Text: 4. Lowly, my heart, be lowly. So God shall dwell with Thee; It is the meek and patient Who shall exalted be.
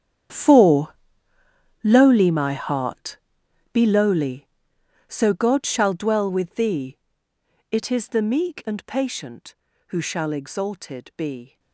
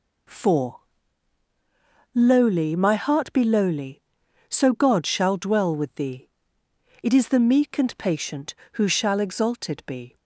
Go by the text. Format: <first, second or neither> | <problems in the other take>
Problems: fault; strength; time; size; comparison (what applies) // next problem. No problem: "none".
second | gets quieter; strong; throughout; 16 dB